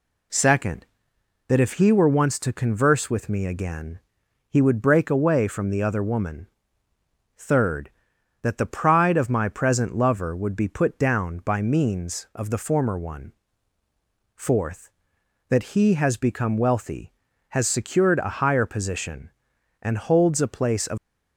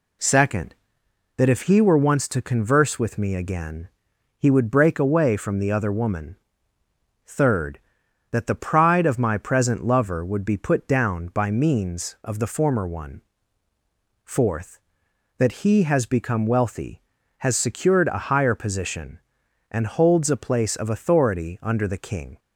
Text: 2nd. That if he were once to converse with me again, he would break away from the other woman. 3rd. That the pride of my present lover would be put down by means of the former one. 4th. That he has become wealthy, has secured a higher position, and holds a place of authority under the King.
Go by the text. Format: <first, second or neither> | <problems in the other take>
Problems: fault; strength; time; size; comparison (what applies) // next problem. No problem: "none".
second | stops before "authority under the King"; at 20.9 s